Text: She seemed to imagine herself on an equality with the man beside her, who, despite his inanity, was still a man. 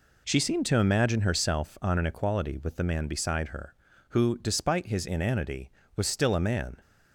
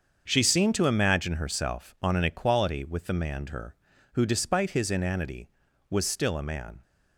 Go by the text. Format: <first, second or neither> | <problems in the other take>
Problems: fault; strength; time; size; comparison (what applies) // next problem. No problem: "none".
first | starts louder than the rest; until 1.2 s; 6.5 dB // skips "beside"; at 3.4 s